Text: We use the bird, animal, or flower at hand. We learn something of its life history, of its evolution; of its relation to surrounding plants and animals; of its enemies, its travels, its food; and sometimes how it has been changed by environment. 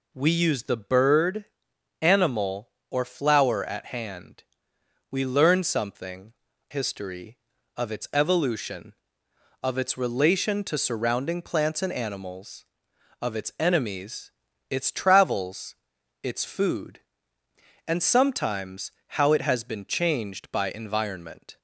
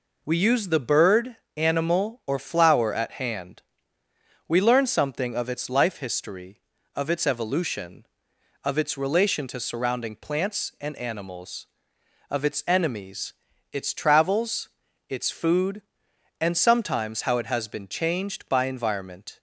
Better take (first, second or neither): second